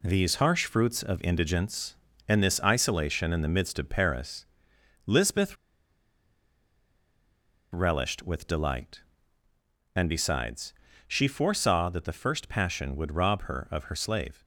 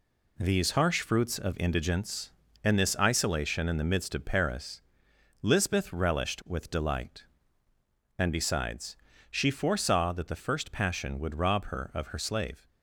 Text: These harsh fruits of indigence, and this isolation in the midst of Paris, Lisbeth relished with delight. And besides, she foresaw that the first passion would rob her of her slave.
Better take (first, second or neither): second